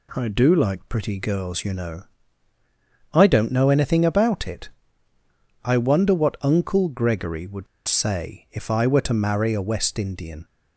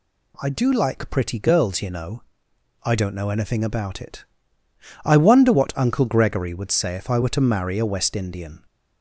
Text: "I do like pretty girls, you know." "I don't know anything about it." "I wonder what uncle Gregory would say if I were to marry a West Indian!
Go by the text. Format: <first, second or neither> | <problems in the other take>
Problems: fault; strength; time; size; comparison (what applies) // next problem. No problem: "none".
second | pauses between "would" and "say"; slight; at 7.6 s; 0.21 s long